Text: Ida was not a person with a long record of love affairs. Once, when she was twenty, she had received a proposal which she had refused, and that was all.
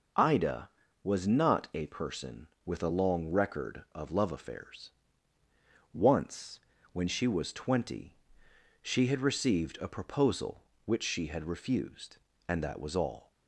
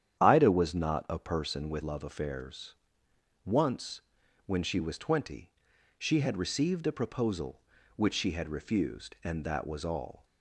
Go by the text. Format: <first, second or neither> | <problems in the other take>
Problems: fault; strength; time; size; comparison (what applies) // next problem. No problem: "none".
first | starts louder than the rest; strong; until 1.2 s; 9.5 dB // skips "a long record of"; at 1.8 s